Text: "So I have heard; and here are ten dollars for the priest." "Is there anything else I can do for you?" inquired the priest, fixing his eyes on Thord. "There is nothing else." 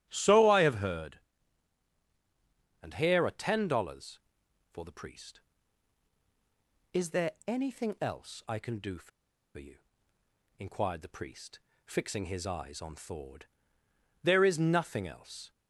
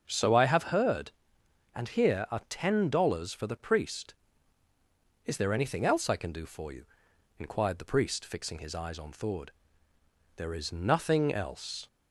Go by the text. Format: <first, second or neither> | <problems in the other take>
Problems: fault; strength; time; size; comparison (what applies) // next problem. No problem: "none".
second | starts louder than the rest; strong; until 1.0 s; 11.5 dB; also in the second // pauses between "for" and "you"; noticeable; at 9.1 s; 0.47 s long